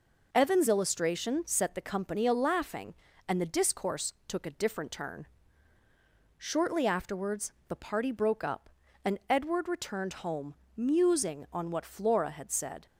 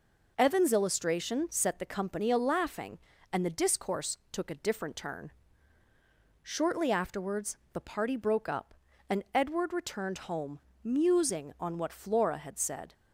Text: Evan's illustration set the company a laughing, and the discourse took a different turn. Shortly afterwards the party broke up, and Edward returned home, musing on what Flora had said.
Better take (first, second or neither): neither